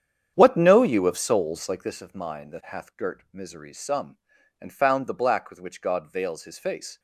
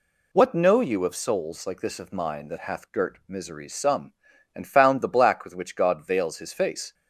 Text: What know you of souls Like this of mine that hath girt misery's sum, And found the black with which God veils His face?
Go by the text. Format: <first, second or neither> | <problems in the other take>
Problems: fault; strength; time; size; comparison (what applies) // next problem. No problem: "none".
second | starts louder than the rest; strong; until 2.0 s; 8.5 dB